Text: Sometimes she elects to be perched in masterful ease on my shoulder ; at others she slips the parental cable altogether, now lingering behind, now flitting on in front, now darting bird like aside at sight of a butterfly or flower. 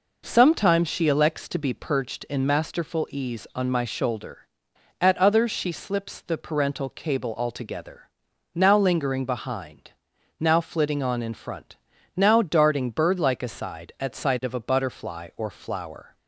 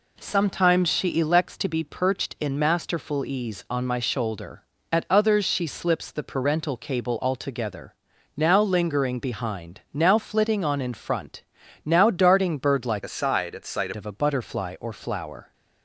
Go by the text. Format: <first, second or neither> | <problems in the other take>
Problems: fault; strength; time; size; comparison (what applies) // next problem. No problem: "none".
first | changes voice from "aside" to "sight"; from 13.0 to 13.9 s; 0.9 s long